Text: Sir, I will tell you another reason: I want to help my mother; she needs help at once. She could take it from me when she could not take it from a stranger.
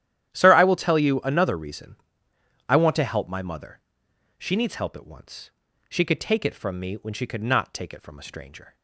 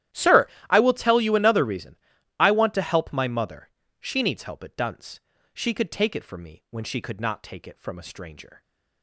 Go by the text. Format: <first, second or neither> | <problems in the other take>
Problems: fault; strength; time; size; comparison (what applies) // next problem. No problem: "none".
first | starts louder than the rest; strong; until 1.3 s; 12.5 dB; strong in the first // says "dunce" for "once"; at 4.7 s